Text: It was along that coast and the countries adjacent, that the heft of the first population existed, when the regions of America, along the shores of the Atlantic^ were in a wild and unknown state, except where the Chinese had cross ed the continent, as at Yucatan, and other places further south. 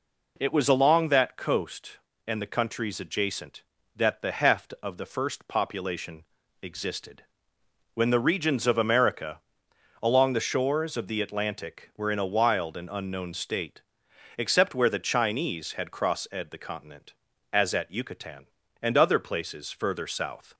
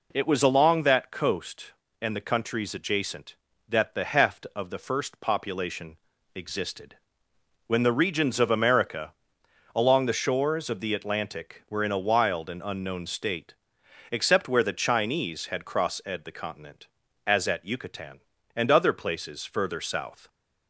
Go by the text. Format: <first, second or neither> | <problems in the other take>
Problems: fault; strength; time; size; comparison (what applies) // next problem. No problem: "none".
neither | pauses between "population" and "existed"; slight; the same in both